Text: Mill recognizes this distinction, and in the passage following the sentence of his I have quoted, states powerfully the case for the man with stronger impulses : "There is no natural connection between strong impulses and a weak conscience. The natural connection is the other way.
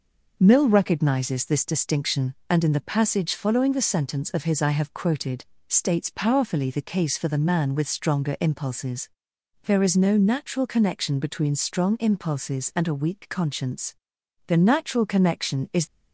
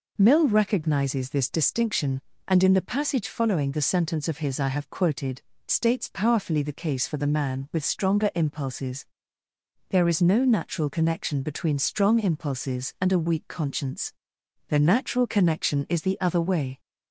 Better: second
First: stops before "the other way"; at 15.8 s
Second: none

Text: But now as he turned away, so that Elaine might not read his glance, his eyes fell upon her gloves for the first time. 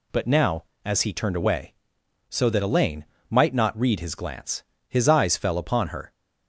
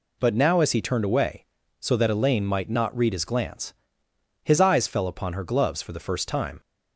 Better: second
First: pauses between "Elaine" and "might"; slight; at 3.0 s; 0.24 s long // stops before "gloves for the first time"; at 6.1 s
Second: none

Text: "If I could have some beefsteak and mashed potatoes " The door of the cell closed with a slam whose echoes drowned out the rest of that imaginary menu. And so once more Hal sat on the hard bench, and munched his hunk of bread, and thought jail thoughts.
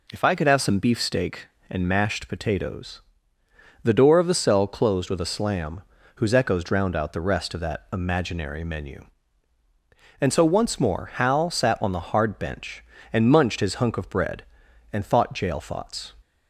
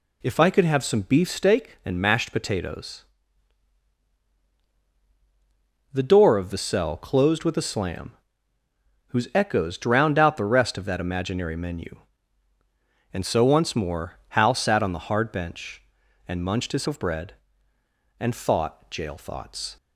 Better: first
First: pauses between "slam" and "whose"; slight; at 5.8 s; 0.36 s long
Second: pauses between "slam" and "whose"; noticeable; at 8.1 s; 0.92 s long // skips "hunk"; at 16.8 s

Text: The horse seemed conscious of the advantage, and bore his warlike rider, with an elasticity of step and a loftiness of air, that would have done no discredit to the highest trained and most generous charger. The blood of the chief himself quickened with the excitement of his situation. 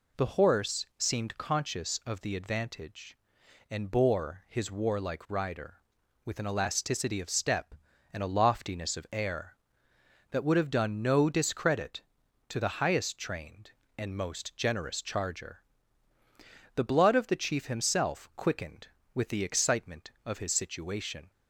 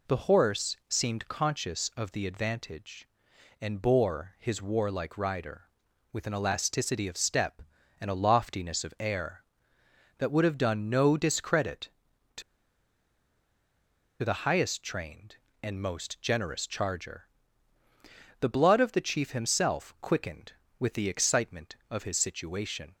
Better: first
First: none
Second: pauses between "to" and "the"; strong; at 12.4 s; 1.8 s long

